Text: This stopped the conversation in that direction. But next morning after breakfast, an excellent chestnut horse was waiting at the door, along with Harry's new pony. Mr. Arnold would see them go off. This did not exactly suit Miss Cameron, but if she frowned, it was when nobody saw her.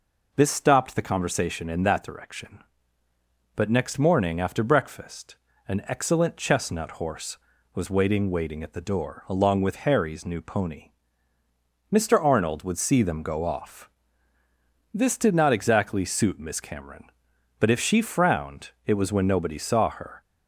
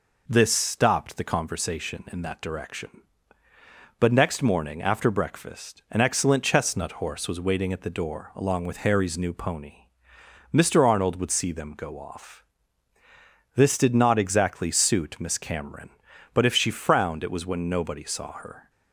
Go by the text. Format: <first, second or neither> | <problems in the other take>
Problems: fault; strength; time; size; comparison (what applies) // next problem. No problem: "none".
second | says "waiting" twice; at 8.3 s